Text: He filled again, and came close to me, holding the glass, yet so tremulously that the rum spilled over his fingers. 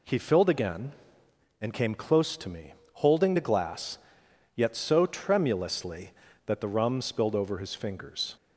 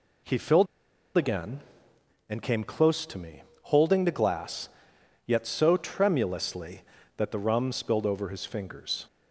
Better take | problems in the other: first | pauses between "filled" and "again"; noticeable; at 0.6 s; 0.51 s long

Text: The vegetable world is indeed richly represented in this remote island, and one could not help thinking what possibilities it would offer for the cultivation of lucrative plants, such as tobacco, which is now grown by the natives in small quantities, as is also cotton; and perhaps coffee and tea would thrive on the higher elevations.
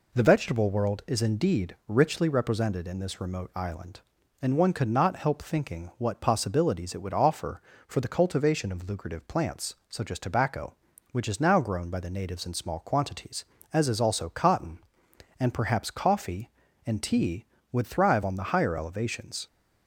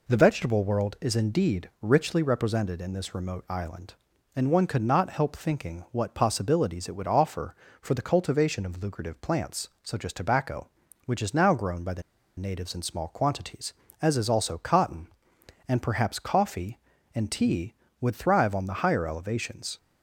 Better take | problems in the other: first | pauses between "the" and "natives"; at 12.0 s; 0.37 s long

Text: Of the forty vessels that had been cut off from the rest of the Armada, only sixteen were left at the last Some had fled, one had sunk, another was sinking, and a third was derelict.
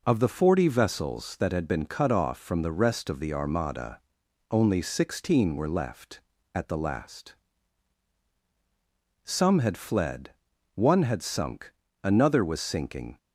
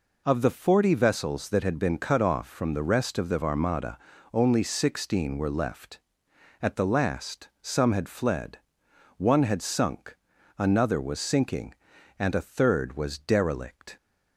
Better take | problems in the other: second | pauses between "last" and "Some"; strong; at 7.3 s; 1.8 s long // stops before "and a third was derelict"; at 13.1 s

